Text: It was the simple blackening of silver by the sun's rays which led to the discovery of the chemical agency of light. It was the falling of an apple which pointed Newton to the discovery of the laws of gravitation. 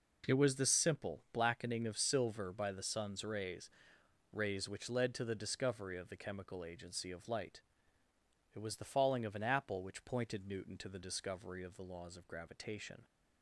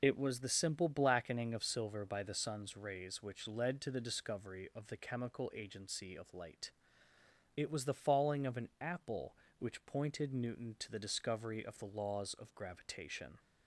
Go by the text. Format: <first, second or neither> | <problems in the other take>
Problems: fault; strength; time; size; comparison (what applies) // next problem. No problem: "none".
second | says "rays" twice; at 4.3 s